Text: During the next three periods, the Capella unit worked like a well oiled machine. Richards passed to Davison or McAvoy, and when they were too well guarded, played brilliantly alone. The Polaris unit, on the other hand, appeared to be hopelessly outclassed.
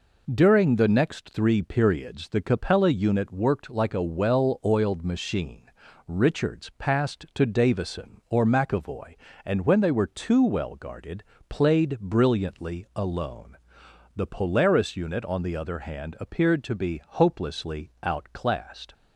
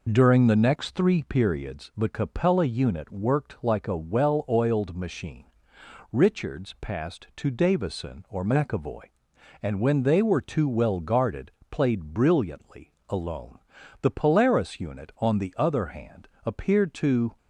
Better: first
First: none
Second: pauses between "brilliantly" and "alone"; slight; at 12.9 s; 0.16 s long // stops before "be hopelessly outclassed"; at 17.3 s

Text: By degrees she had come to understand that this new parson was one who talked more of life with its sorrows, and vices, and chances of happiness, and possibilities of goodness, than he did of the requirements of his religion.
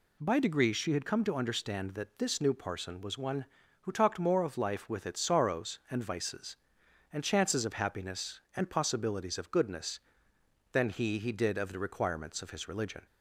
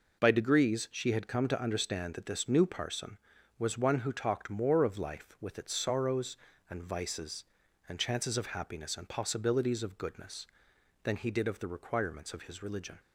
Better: second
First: says "he" twice; at 11.1 s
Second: none

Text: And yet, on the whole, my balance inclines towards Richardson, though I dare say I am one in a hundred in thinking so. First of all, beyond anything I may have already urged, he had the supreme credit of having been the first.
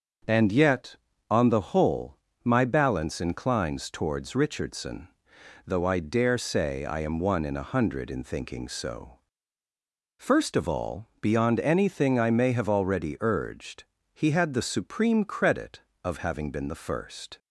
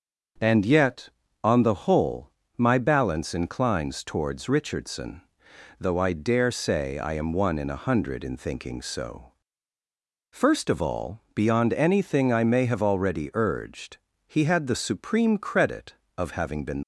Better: first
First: starts louder than the rest; until 1.6 s; 6.5 dB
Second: starts louder than the rest; until 1.7 s; 6.5 dB // stops before "the first"; at 16.8 s

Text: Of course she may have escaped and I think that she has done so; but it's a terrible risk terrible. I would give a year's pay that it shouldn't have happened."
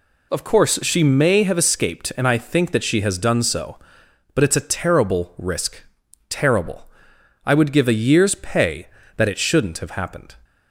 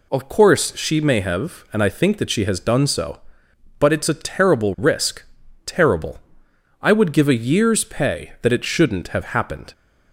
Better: first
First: pauses between "risk" and "terrible"; noticeable; at 5.8 s; 0.46 s long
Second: skips "escaped"; at 1.6 s // pauses between "risk" and "terrible"; at 5.2 s; 0.42 s long

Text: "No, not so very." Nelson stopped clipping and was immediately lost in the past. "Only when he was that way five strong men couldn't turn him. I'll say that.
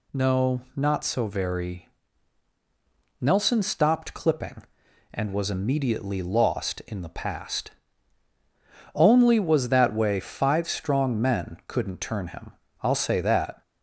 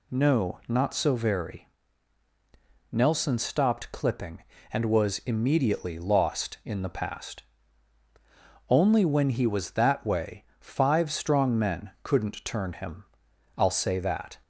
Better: second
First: skips "when he"; at 9.3 s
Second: none

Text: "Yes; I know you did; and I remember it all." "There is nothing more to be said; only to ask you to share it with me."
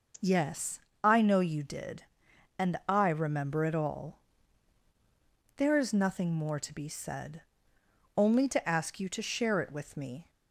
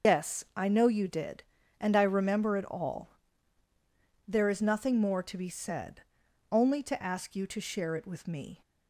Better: first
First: none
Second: loses the start of "Yes"; at 0.0 s; 140 ms // starts louder than the rest; until 1.1 s; 6 dB

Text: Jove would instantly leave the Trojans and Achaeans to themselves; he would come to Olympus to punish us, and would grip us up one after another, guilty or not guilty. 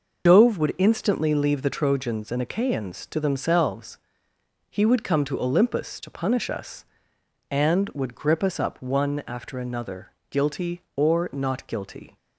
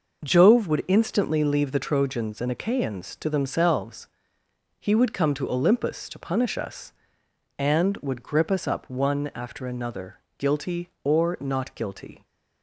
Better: second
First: loses the start of "Jove"; at 0.2 s; 120 ms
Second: none

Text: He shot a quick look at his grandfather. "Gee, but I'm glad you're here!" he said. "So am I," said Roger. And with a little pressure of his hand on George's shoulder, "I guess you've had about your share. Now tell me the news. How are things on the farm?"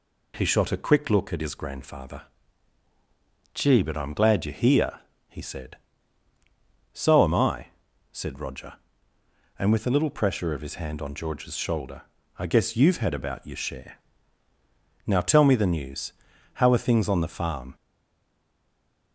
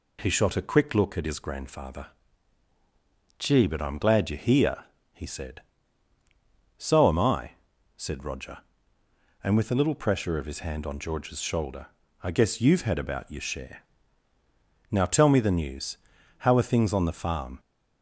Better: second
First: stays silent after the last word; noticeable; from 17.7 s on; 1.4 s long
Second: none

